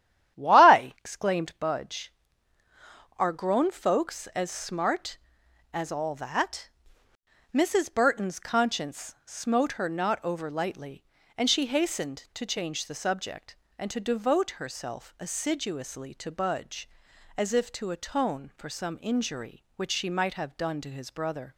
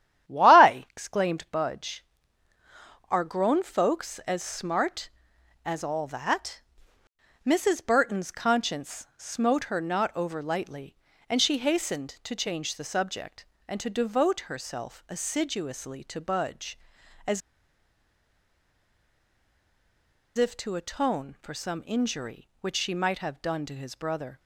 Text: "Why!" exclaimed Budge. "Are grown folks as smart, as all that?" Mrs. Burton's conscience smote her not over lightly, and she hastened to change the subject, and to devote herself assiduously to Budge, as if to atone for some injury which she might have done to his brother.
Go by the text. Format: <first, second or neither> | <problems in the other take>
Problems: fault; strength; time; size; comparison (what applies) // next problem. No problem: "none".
first | starts louder than the rest; strong; until 1.3 s; 11 dB; strong in the first // pauses between "as" and "if"; strong; at 17.4 s; 2.9 s long